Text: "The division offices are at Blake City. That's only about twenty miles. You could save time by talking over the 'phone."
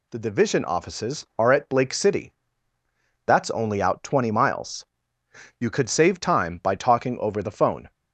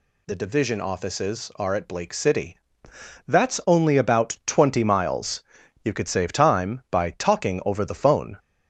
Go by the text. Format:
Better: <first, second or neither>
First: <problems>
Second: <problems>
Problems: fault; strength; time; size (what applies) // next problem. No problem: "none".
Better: second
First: says "out" for "about"; at 3.8 s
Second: none